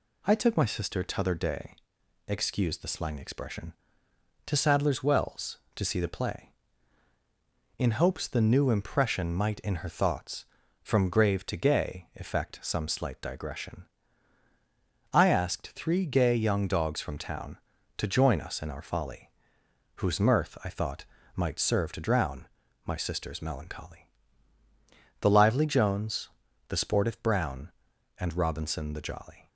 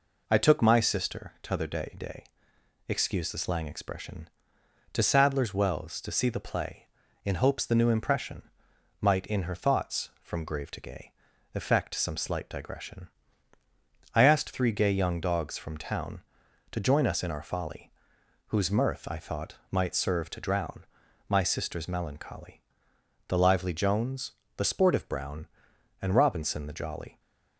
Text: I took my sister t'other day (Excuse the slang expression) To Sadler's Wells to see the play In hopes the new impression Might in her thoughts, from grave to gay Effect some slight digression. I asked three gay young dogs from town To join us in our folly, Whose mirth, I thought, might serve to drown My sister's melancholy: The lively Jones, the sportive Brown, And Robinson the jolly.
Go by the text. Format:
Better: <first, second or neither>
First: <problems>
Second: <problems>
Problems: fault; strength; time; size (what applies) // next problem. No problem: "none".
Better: first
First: pauses between "drown" and "My"; at 22.4 s; 0.40 s long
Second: says "day" twice; at 1.9 s // pauses between "impression" and "Might"; noticeable; at 8.4 s; 0.58 s long // pauses between "gay" and "Effect"; at 11.1 s; 0.42 s long // pauses between "drown" and "My"; at 20.8 s; 0.44 s long